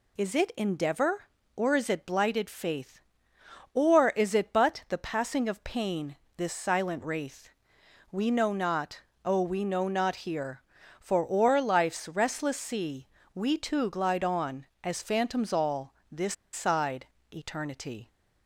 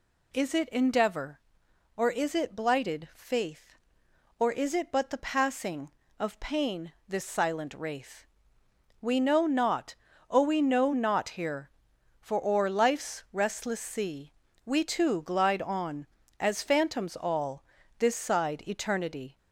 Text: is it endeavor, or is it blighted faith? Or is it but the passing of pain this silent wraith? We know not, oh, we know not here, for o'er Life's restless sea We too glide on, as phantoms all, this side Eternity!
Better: second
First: pauses between "pain" and "this"; slight; at 6.1 s; 0.22 s long // pauses between "sea" and "We"; slight; at 13.0 s; 0.26 s long // pauses between "this" and "side"; slight; at 16.3 s; 0.19 s long // pauses between "side" and "Eternity"; slight; at 17.0 s; 0.26 s long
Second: pauses between "sea" and "We"; slight; at 14.3 s; 0.32 s long

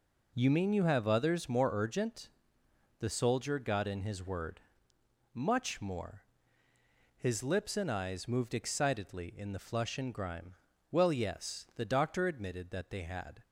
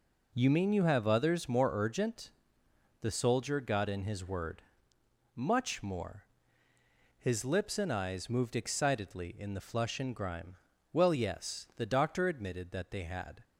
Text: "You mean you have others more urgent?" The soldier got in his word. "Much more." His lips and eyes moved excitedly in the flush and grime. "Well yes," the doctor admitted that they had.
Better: neither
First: none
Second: none

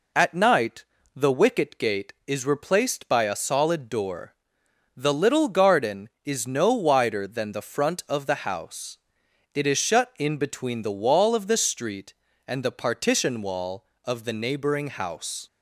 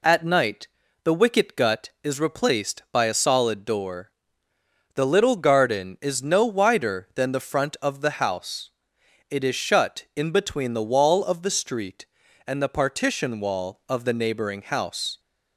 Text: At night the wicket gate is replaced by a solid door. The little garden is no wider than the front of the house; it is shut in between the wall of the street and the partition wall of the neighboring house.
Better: first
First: pauses between "night" and "the"; slight; at 0.8 s; 0.30 s long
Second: pauses between "night" and "the"; slight; at 0.6 s; 0.36 s long // says "gut" for "gate"; at 1.5 s

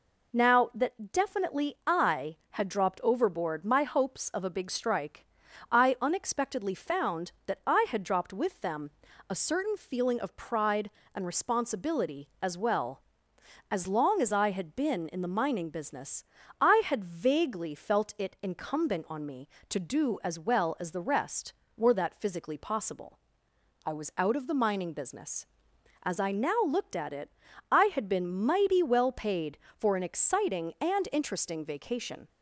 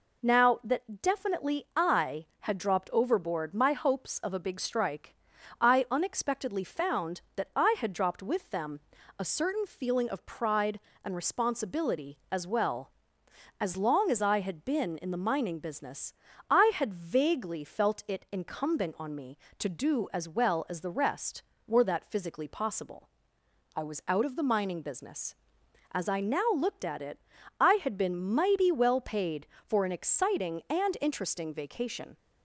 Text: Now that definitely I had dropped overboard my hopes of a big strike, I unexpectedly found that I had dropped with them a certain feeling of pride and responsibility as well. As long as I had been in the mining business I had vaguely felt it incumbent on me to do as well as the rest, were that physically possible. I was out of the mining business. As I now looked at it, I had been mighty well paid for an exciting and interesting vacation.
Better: neither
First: pauses between "them" and "a"; at 8.9 s; 0.38 s long // pauses between "business" and "I"; slight; at 16.2 s; 0.36 s long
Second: pauses between "them" and "a"; at 8.7 s; 0.38 s long // pauses between "business" and "I"; slight; at 16.1 s; 0.36 s long

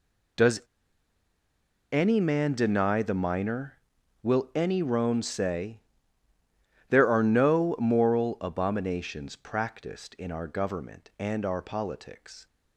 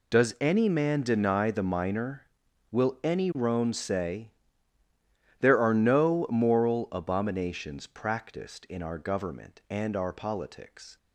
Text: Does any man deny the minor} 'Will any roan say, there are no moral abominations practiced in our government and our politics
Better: second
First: pauses between "Does" and "any"; strong; at 0.6 s; 1.3 s long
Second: none

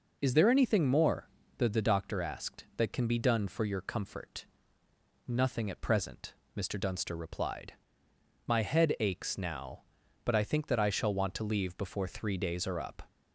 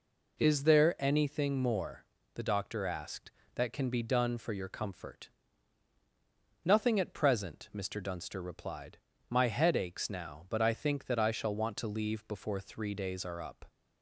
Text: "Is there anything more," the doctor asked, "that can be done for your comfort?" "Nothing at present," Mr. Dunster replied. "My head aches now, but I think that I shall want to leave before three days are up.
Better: second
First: says "the" twice; at 1.6 s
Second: none

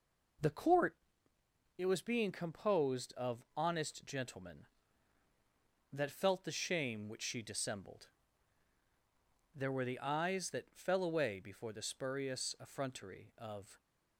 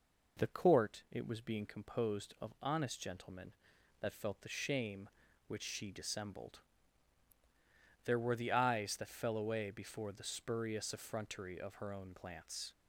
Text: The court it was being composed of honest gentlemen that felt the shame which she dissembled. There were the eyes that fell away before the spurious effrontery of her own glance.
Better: second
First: pauses between "court" and "it"; noticeable; at 0.9 s; 0.82 s long // stops before "her own glance"; at 13.7 s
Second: none

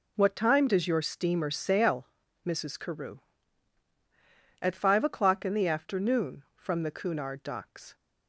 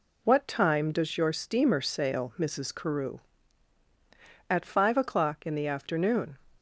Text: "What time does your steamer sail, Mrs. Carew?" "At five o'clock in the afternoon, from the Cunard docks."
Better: first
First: none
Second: stops before "from the Cunard docks"; at 6.5 s

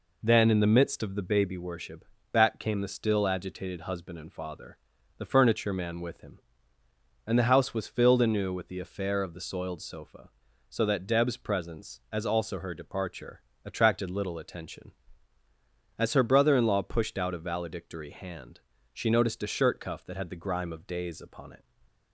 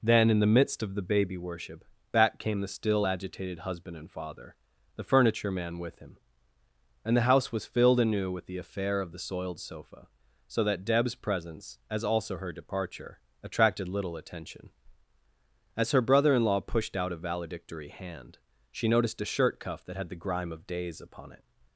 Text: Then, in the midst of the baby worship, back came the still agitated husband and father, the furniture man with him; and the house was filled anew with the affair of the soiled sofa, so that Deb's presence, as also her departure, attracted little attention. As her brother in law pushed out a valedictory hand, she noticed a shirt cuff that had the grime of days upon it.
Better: neither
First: none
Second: none

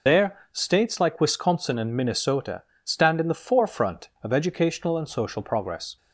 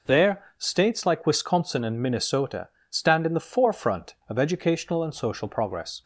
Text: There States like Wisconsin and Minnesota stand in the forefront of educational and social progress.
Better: second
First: loses the start of "There"; at 0.0 s; 55 ms // pauses between "There" and "States"; slight; at 0.3 s; 0.16 s long // pauses between "Minnesota" and "stand"; slight; at 2.6 s; 0.22 s long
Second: pauses between "There" and "States"; slight; at 0.4 s; 0.16 s long // pauses between "Minnesota" and "stand"; slight; at 2.6 s; 0.22 s long

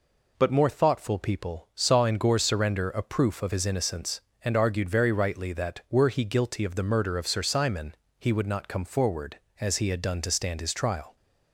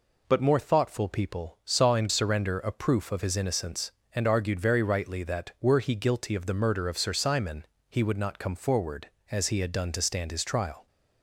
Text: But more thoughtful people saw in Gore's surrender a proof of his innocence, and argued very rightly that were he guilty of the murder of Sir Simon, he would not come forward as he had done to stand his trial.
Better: first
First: none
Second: skips "Gore's"; at 2.0 s

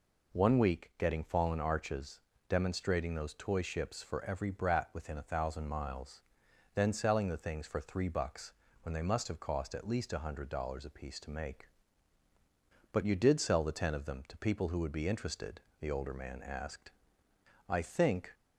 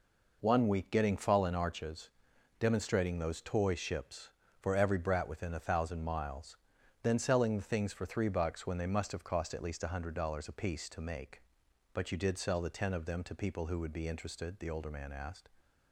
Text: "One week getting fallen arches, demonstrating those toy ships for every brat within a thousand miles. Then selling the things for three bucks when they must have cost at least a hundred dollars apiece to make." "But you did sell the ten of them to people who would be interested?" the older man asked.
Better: second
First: pauses between "bucks" and "when"; slight; at 8.5 s; 0.28 s long // goes on to say "I think"; noticeable; from 17.6 s on; 0.66 s long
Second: none

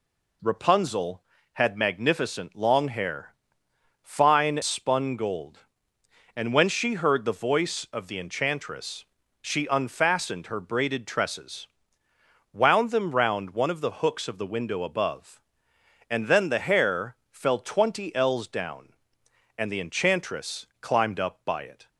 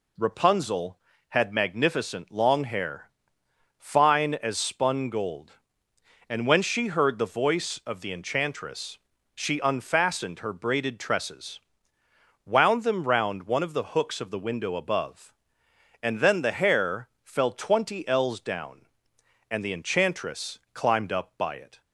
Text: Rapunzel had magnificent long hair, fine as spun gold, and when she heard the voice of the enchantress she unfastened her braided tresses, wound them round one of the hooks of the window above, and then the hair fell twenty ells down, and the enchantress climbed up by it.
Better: second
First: skips "as"; at 4.6 s // pauses between "enchantress" and "she"; at 9.0 s; 0.40 s long // pauses between "hair" and "fell"; slight; at 17.1 s; 0.16 s long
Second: pauses between "enchantress" and "she"; at 8.9 s; 0.40 s long // pauses between "hair" and "fell"; slight; at 17.0 s; 0.16 s long

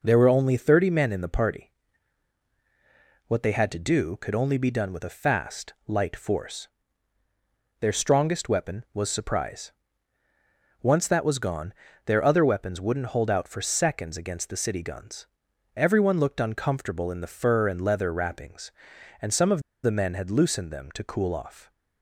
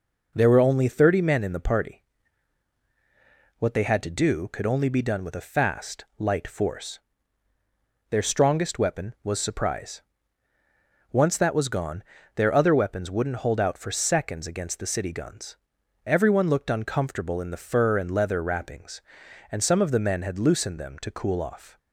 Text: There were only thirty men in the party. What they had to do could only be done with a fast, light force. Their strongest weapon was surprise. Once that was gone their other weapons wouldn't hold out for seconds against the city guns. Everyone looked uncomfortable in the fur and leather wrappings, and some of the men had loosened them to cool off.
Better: second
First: pauses between "gone" and "their"; slight; at 11.7 s; 0.34 s long // pauses between "of" and "the"; slight; at 19.6 s; 0.22 s long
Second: pauses between "gone" and "their"; slight; at 12.0 s; 0.34 s long

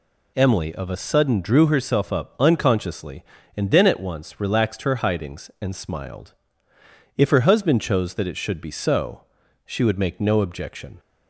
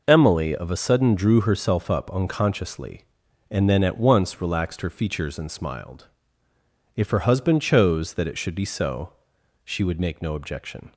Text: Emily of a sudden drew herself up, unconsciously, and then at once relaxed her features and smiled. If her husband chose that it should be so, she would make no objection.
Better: second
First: says "hidings" for "features"; at 4.9 s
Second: none

